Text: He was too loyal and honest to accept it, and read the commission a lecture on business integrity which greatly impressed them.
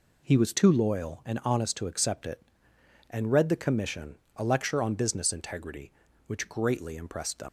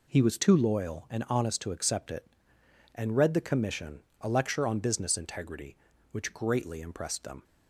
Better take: second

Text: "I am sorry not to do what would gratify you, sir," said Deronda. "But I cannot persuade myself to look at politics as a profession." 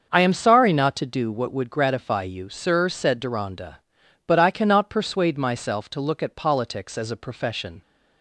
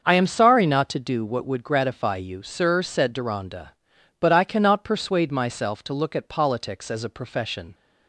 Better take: neither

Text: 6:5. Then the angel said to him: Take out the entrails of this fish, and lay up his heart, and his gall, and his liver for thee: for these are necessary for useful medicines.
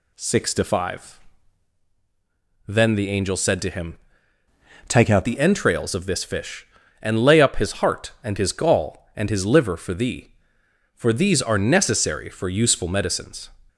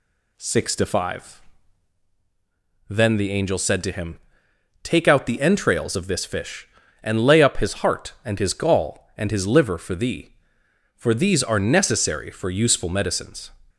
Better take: second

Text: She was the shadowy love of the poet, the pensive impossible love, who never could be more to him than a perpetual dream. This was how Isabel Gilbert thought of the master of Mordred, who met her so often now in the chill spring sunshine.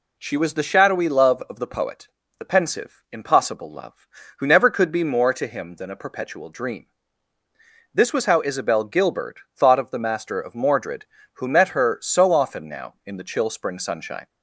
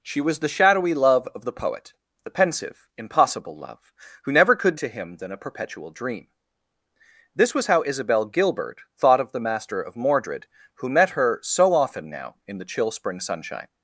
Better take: first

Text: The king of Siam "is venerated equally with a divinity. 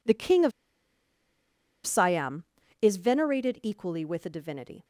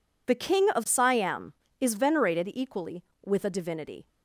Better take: second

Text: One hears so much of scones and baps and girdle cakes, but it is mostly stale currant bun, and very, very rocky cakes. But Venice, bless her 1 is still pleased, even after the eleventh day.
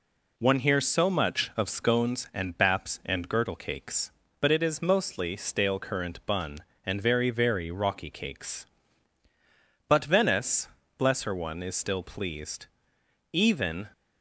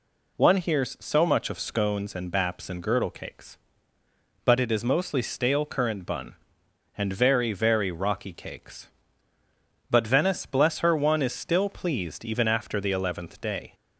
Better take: second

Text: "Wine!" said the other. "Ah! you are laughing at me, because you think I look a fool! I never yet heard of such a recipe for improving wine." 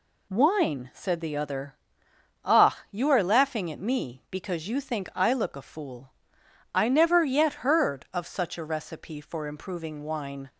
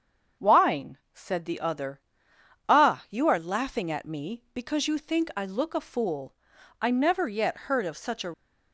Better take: first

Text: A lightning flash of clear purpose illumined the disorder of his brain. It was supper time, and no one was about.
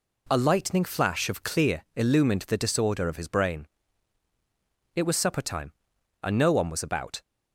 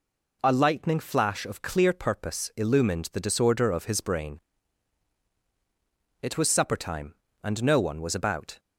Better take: second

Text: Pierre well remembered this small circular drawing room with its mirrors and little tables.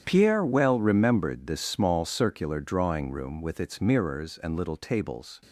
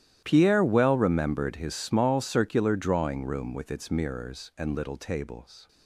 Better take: first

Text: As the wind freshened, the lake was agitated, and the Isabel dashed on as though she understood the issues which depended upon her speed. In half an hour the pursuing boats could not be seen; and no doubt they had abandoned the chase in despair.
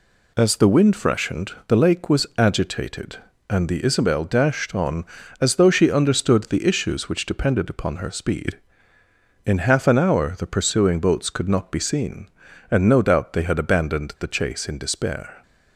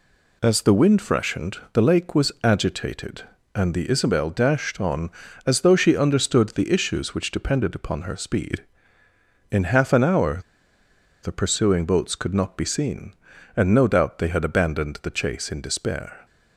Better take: first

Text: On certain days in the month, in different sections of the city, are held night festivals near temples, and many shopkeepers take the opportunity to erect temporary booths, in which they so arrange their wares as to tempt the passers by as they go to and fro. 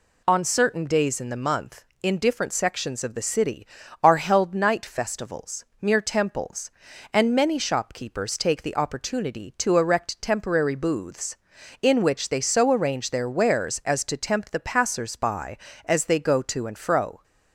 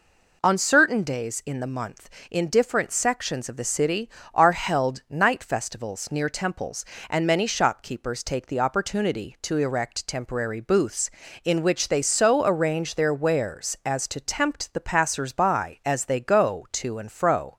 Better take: second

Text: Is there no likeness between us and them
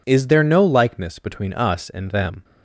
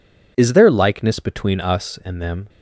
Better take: first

